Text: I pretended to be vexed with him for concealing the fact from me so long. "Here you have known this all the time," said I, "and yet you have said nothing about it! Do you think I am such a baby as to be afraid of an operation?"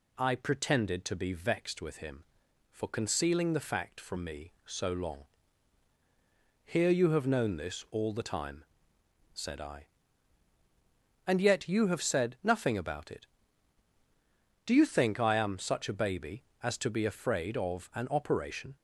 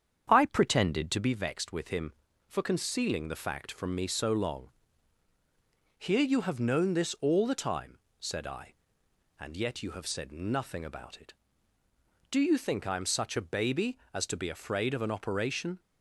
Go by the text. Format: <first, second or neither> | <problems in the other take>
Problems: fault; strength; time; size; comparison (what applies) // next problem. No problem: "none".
first | starts louder than the rest; strong; until 1.3 s; 8 dB